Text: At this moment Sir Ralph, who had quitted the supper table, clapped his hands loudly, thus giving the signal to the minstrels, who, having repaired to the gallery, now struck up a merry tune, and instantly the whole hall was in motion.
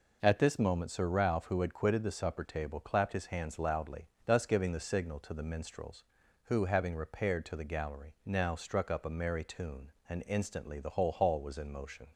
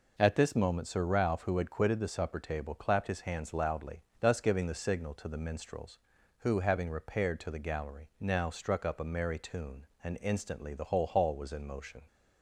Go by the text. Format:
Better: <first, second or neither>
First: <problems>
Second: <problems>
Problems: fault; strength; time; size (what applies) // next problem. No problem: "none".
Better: neither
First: none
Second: none